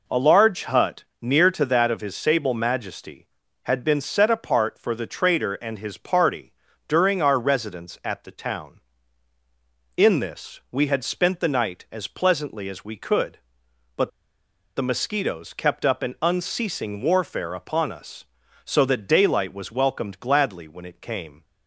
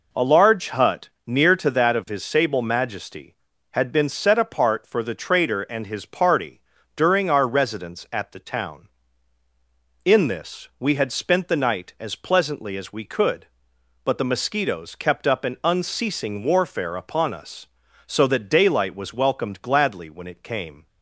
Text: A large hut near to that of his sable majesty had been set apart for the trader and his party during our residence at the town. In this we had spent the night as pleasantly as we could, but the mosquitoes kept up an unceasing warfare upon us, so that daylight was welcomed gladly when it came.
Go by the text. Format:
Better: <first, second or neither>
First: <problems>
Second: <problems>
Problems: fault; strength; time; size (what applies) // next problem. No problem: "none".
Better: second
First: pauses between "hut" and "near"; slight; at 1.0 s; 0.18 s long // pauses between "party" and "during"; slight; at 6.5 s; 0.34 s long // pauses between "but" and "the"; noticeable; at 14.0 s; 0.66 s long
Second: pauses between "hut" and "near"; slight; at 1.0 s; 0.18 s long // pauses between "party" and "during"; slight; at 6.5 s; 0.34 s long